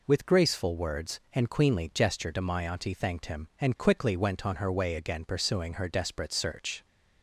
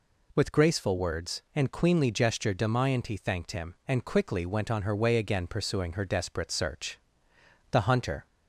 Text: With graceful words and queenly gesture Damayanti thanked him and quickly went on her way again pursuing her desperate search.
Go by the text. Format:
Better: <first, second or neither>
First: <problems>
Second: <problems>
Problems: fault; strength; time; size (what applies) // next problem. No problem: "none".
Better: first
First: none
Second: goes on to say "The hunter"; from 7.7 s on; 0.54 s long